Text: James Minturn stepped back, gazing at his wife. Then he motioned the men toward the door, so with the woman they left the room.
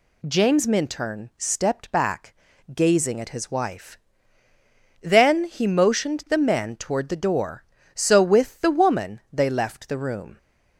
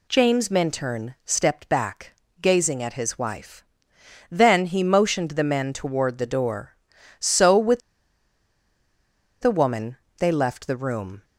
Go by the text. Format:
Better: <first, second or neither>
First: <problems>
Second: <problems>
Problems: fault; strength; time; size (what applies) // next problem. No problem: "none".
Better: first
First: none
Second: pauses between "with" and "the"; strong; at 7.7 s; 1.6 s long // pauses between "woman" and "they"; slight; at 9.9 s; 0.22 s long